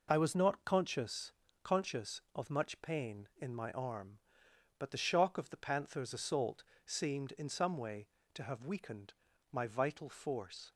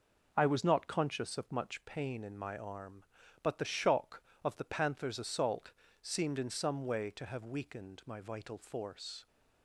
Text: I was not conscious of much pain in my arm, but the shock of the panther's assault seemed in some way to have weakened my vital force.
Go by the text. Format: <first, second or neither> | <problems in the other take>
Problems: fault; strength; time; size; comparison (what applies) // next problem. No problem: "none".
second | says "conscious" twice; at 1.6 s // pauses between "assault" and "seemed"; slight; at 6.6 s; 0.20 s long; slight in the second // pauses between "weakened" and "my"; at 9.1 s; 0.38 s long